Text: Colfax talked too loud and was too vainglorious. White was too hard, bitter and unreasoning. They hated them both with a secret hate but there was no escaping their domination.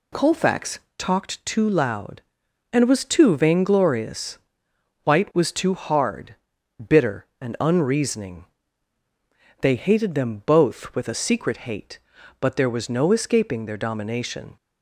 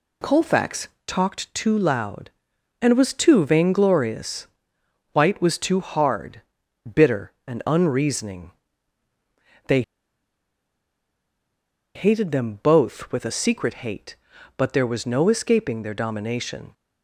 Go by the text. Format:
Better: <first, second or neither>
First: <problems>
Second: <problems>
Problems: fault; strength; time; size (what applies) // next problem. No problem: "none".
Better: first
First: pauses between "Colfax" and "talked"; slight; at 0.7 s; 0.18 s long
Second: pauses between "Colfax" and "talked"; slight; at 0.8 s; 0.18 s long // pauses between "They" and "hated"; strong; at 9.8 s; 2.1 s long